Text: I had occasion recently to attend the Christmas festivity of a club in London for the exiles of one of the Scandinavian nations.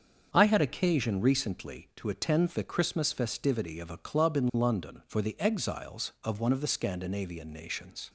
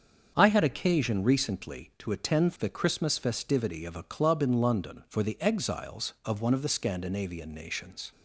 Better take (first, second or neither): neither